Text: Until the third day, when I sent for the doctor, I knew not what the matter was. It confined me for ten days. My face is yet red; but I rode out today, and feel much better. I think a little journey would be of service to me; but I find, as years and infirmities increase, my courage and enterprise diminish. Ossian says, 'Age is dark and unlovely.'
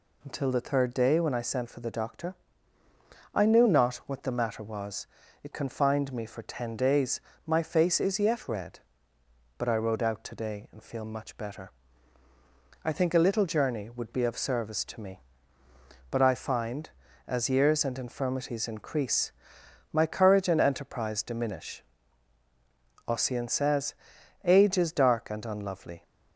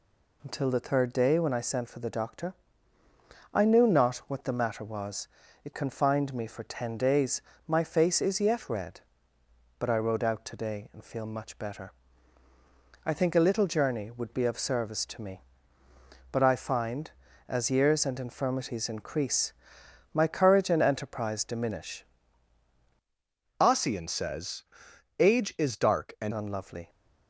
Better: first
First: none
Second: changes voice from "Ossian" to "and"; from 23.5 to 26.3 s; 2.8 s long

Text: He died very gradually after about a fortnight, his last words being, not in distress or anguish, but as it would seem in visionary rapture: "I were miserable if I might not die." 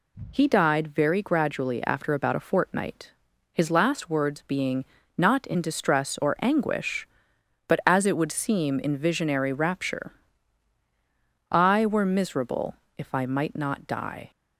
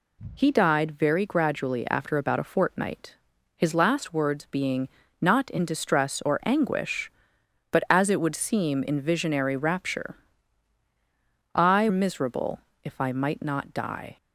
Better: first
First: pauses between "miserable" and "if"; slight; at 12.7 s; 0.20 s long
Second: skips "were"; at 11.8 s // pauses between "miserable" and "if"; slight; at 12.6 s; 0.22 s long

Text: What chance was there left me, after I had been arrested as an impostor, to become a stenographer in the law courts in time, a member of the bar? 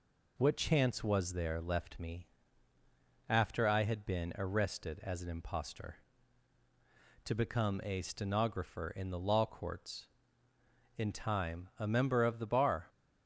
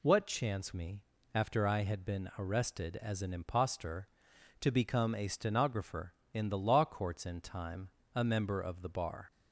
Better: first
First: none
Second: skips "was there left"; at 0.7 s

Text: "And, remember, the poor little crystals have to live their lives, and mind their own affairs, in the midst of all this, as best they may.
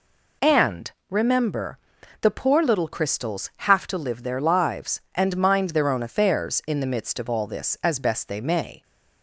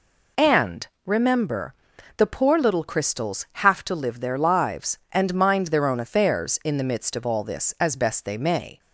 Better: neither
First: none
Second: none

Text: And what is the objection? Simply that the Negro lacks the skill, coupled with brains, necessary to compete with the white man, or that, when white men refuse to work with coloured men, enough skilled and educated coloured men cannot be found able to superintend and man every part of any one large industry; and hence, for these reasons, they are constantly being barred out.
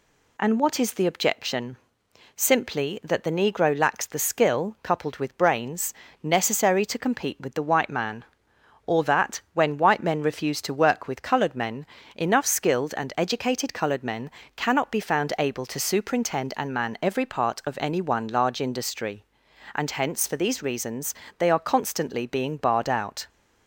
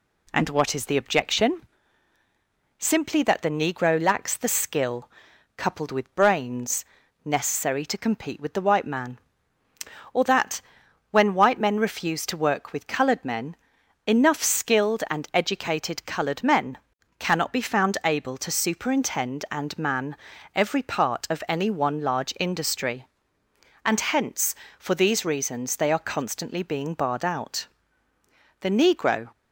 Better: first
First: pauses between "men" and "cannot"; slight; at 14.2 s; 0.26 s long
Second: pauses between "men" and "cannot"; at 16.7 s; 0.42 s long // pauses between "man" and "every"; at 20.1 s; 0.40 s long // goes on to say "The Negro"; noticeable; from 28.6 s on; 0.70 s long

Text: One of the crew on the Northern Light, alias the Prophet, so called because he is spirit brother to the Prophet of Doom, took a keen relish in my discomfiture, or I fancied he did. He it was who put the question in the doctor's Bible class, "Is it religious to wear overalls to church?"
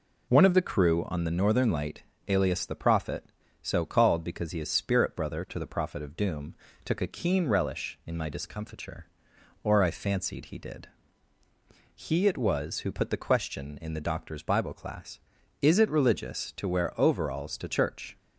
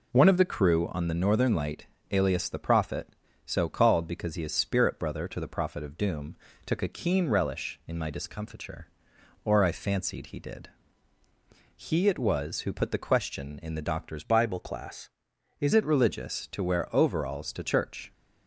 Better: first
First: none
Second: changes voice from "Bible" to "Is"; from 14.2 to 15.7 s; 1.5 s long

